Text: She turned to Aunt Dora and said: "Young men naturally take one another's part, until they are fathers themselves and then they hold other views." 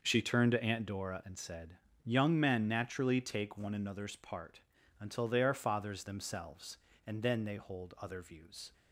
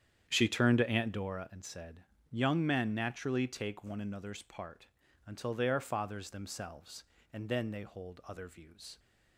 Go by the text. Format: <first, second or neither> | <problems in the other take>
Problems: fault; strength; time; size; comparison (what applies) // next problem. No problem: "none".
first | starts louder than the rest; strong; until 1.4 s; 9 dB